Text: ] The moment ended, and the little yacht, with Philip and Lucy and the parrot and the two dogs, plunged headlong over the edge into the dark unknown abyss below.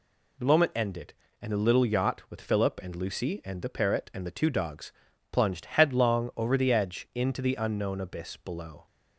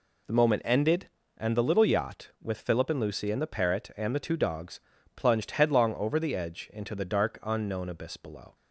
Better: second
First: skips "dark"; at 7.5 s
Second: none

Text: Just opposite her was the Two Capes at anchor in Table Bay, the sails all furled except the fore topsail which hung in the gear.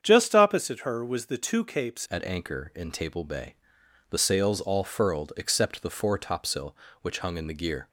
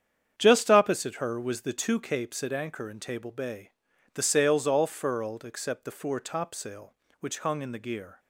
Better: second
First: starts louder than the rest; strong; until 1.0 s; 8 dB // changes voice at "at"; from 2.1 s on; 5.7 s long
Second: starts louder than the rest; strong; until 1.3 s; 8.5 dB

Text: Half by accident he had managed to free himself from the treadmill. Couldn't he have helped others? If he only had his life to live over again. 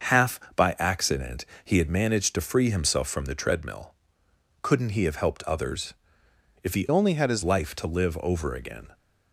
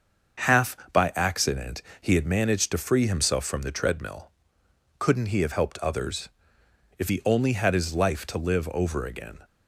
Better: second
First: starts louder than the rest; until 1.2 s; 6.5 dB // pauses between "accident" and "he"; slight; at 1.4 s; 0.18 s long // changes voice from "only" to "his"; from 6.9 to 7.4 s; 0.5 s long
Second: starts louder than the rest; until 1.6 s; 6.5 dB // pauses between "accident" and "he"; slight; at 1.8 s; 0.18 s long

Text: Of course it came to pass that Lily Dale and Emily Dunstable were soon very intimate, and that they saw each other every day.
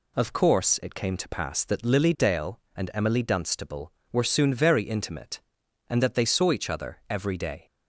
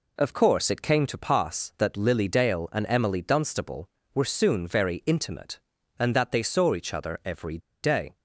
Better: first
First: none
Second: pauses between "every" and "day"; slight; at 7.5 s; 0.24 s long

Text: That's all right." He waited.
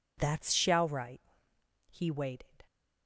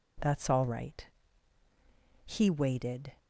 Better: second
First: says "shall" for "all"; at 0.5 s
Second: none

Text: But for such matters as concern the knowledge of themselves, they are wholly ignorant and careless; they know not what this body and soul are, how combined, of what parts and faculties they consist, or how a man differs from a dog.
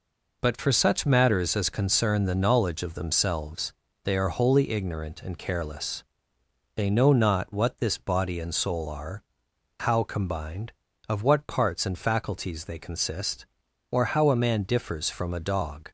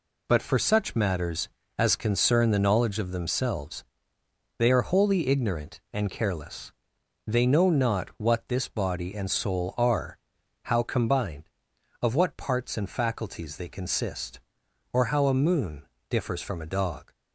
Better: first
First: none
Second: says "moon" for "man"; at 15.3 s

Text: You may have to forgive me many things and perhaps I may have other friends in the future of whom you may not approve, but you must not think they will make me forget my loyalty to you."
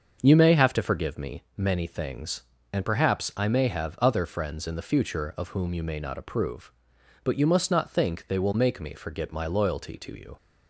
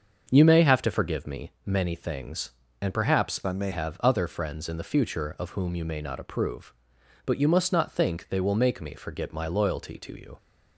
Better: first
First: starts louder than the rest; until 1.2 s; 6.5 dB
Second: starts louder than the rest; until 1.3 s; 6.5 dB // changes voice from "I" to "may"; from 3.4 to 3.7 s; 0.3 s long

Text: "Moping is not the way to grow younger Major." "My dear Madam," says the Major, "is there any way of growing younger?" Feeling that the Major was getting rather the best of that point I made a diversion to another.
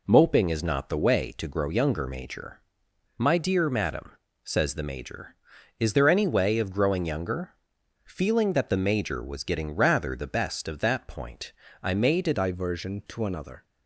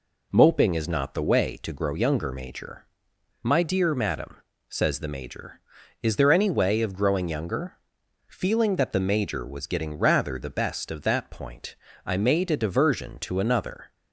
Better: second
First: pauses between "point" and "I"; slight; at 11.5 s; 0.28 s long // changes voice at "diversion"; from 12.3 s on; 1.3 s long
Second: pauses between "point" and "I"; slight; at 11.7 s; 0.28 s long

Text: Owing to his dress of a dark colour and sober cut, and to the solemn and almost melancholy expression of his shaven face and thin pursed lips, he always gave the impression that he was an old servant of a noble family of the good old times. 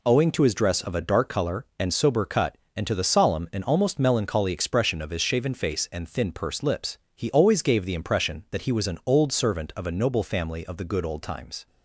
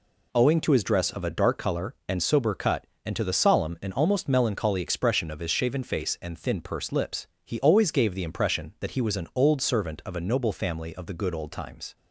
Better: neither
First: none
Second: none

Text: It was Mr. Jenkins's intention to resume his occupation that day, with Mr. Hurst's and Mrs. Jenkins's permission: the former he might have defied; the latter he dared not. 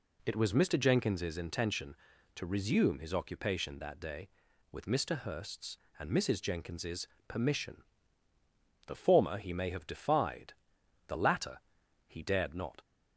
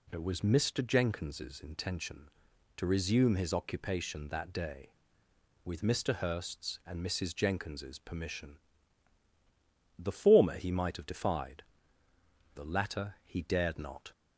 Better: second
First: pauses between "Jenkins's" and "permission"; slight; at 7.0 s; 0.20 s long // says "may" for "might"; at 9.5 s // pauses between "latter" and "he"; noticeable; at 11.5 s; 0.48 s long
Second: none

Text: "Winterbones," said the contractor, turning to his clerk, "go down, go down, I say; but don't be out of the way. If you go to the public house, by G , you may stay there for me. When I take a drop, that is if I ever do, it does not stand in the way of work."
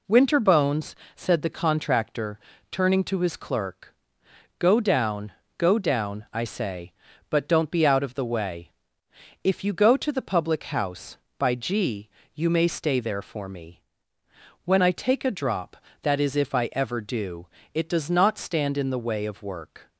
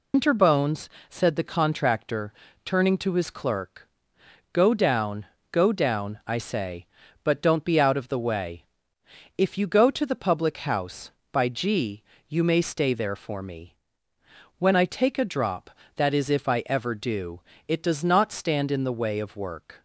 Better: first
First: none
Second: loses the start of "Winterbones"; at 0.1 s; 135 ms

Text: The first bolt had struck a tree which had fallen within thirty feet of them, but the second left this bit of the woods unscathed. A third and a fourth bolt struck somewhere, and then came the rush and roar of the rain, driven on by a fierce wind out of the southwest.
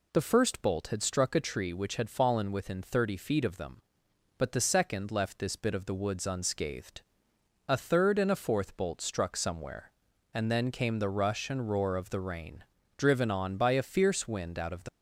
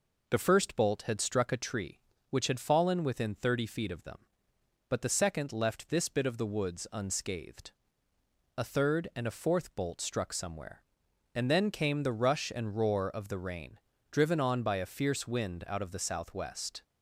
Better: second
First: stops before "southwest"; at 14.8 s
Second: none

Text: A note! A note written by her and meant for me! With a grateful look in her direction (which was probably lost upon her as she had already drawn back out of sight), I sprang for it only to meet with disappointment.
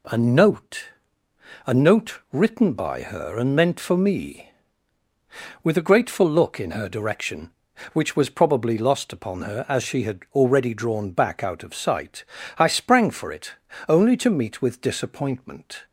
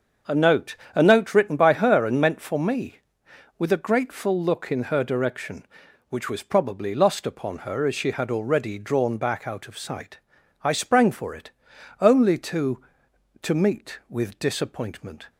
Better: first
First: pauses between "it" and "only"; slight; at 13.5 s; 0.36 s long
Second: starts louder than the rest; until 1.4 s; 7 dB // pauses between "it" and "only"; noticeable; at 11.5 s; 0.50 s long // says "to" twice; at 13.4 s

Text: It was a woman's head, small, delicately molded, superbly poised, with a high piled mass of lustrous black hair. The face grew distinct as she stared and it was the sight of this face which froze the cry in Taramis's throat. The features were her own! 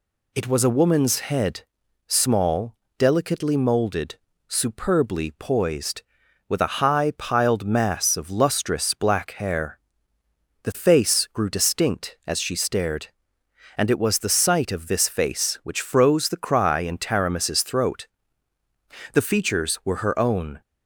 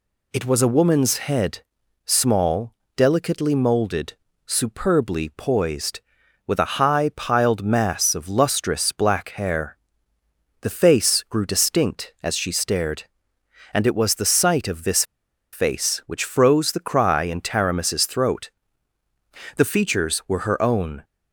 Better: first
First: none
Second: pauses between "this" and "face"; noticeable; at 15.0 s; 0.47 s long

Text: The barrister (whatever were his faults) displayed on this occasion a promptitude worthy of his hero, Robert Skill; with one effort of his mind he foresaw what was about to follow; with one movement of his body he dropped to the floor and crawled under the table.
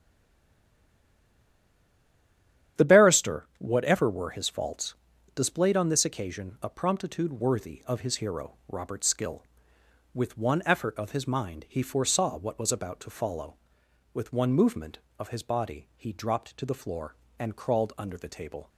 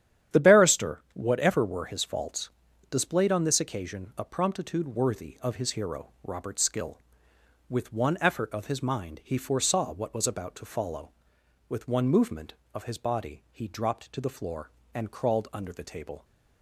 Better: second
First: stays silent before the first word; strong; until 2.7 s; 2.7 s long // starts louder than the rest; strong; until 3.8 s; 10 dB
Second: starts louder than the rest; strong; until 1.4 s; 10 dB

